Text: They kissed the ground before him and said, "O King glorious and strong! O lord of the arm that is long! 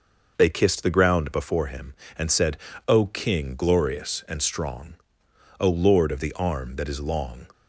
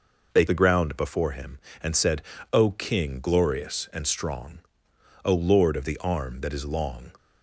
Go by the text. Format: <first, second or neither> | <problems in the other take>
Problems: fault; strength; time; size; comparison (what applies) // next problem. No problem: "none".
first | skips "kissed"; at 0.4 s